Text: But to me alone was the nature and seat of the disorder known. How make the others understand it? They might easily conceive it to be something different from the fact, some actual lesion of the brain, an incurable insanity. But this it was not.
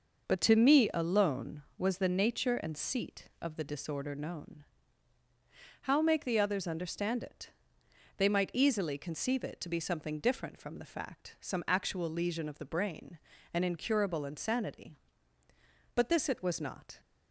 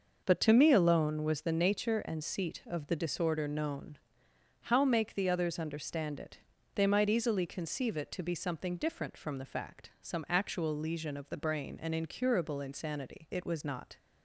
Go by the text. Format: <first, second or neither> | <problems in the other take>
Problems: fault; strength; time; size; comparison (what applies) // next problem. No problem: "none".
first | skips "But this"; at 13.2 s